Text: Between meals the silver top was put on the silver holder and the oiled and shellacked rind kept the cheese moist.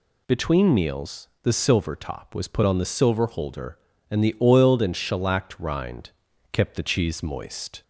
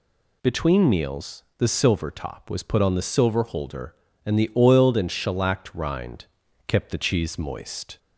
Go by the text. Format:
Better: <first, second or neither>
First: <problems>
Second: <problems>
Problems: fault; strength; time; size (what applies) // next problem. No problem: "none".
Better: neither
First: pauses between "rind" and "kept"; at 6.1 s; 0.42 s long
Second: pauses between "rind" and "kept"; at 6.2 s; 0.42 s long